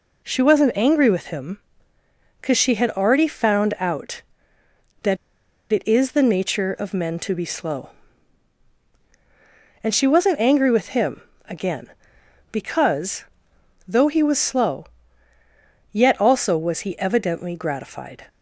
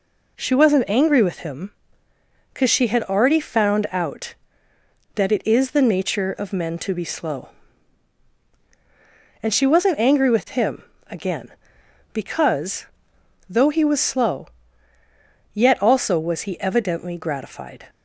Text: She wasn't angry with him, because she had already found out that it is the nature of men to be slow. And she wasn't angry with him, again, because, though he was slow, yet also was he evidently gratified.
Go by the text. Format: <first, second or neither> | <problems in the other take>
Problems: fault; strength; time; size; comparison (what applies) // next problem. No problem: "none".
second | pauses between "that" and "it"; noticeable; at 5.1 s; 0.54 s long